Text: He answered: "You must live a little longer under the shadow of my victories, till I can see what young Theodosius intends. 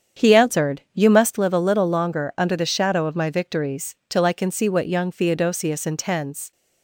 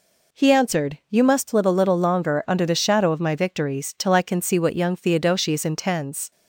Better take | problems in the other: second | starts louder than the rest; strong; until 1.4 s; 8 dB

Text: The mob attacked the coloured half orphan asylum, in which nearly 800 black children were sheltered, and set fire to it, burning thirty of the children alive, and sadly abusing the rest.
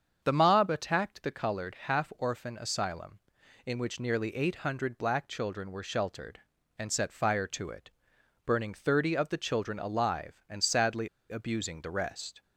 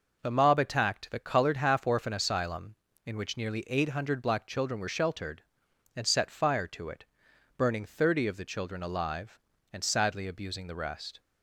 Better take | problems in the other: second | starts louder than the rest; strong; until 1.2 s; 7 dB // pauses between "sadly" and "abusing"; slight; at 11.0 s; 0.21 s long

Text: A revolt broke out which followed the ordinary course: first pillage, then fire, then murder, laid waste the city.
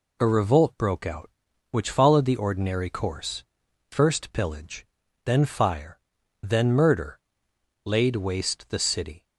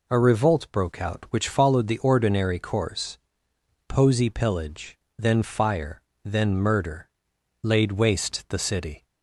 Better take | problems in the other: first | says "posey" for "first"; at 3.8 s

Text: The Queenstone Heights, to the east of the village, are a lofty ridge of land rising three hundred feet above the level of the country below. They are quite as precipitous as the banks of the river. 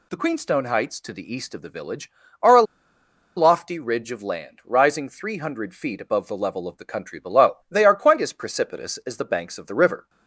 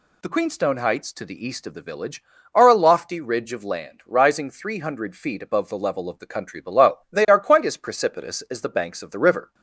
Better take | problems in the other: second | pauses between "a" and "lofty"; noticeable; at 2.6 s; 0.73 s long

